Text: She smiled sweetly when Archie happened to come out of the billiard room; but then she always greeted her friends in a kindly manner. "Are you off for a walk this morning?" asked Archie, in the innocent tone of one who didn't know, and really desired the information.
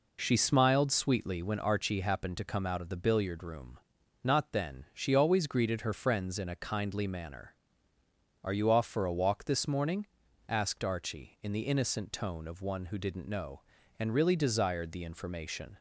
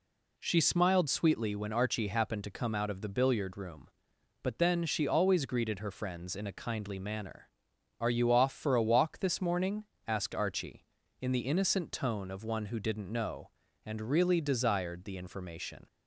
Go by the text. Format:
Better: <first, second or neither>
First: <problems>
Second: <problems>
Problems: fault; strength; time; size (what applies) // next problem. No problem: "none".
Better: second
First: says "not" for "but"; at 4.2 s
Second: none